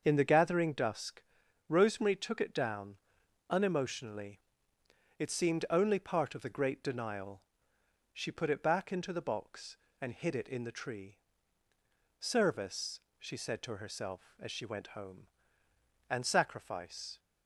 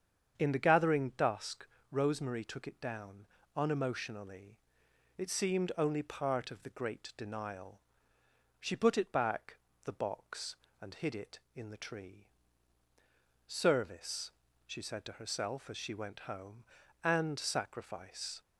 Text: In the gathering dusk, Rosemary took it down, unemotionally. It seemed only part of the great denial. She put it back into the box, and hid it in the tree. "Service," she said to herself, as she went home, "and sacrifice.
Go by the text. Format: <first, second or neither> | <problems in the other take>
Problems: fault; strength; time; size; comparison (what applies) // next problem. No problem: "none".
first | starts louder than the rest; strong; until 1.3 s; 7.5 dB; also in the first // skips "into"; at 9.7 s